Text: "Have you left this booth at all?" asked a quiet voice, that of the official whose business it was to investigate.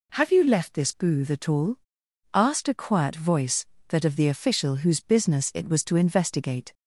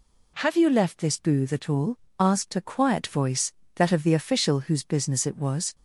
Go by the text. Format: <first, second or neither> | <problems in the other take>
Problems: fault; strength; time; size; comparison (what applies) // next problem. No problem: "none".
first | stops before "to investigate"; at 5.7 s